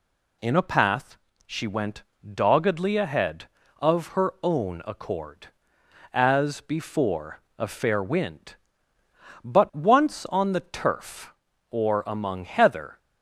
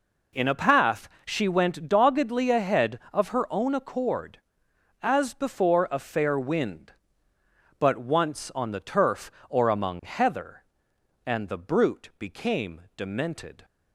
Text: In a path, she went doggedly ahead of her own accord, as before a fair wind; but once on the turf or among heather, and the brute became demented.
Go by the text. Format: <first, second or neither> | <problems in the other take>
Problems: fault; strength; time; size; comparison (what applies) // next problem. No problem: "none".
second | pauses between "went" and "doggedly"; slight; at 2.0 s; 0.20 s long // pauses between "before" and "a"; slight; at 7.4 s; 0.16 s long // stops before "and the brute became demented"; at 12.9 s